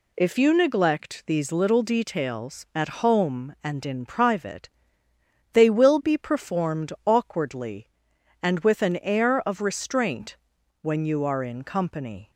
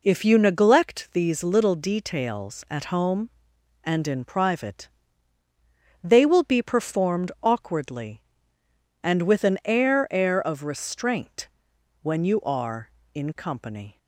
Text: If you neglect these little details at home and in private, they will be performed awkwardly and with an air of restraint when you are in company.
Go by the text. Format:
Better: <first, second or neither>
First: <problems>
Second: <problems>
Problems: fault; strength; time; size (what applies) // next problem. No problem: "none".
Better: first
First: pauses between "restraint" and "when"; at 10.3 s; 0.42 s long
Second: says "air" twice; at 10.1 s // pauses between "restraint" and "when"; noticeable; at 11.4 s; 0.54 s long